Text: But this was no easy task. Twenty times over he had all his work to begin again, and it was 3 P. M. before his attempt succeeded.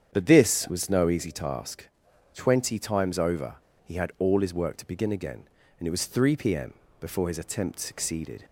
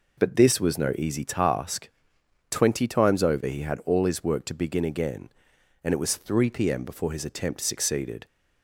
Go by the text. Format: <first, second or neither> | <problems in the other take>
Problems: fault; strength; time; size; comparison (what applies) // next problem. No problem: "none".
second | starts louder than the rest; strong; until 1.1 s; 8 dB // pauses between "over" and "he"; slight; at 3.5 s; 0.29 s long // pauses between "M" and "before"; slight; at 6.7 s; 0.26 s long